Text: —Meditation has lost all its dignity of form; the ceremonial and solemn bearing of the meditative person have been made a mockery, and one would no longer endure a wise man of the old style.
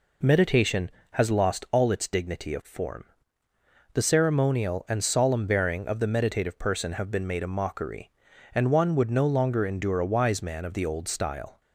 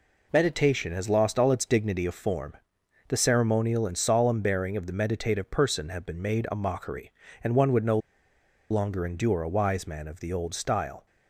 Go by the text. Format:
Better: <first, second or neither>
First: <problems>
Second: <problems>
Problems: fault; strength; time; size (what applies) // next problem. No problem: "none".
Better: first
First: none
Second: pauses between "no" and "longer"; noticeable; at 7.9 s; 0.72 s long